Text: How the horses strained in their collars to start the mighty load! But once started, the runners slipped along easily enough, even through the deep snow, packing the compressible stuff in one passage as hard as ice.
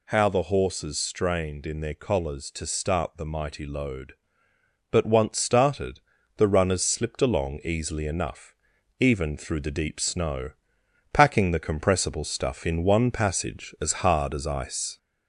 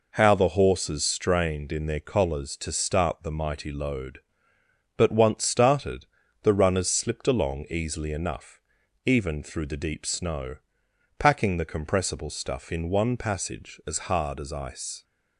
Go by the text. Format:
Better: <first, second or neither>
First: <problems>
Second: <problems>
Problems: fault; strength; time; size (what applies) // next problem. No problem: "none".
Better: second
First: gets louder; slight; throughout; 2.5 dB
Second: none